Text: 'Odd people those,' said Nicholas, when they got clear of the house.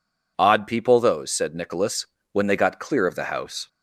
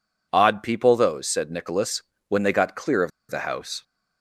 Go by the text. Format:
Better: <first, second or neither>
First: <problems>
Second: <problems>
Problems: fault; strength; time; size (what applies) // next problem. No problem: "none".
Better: first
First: none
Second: pauses between "of" and "the"; slight; at 3.1 s; 0.20 s long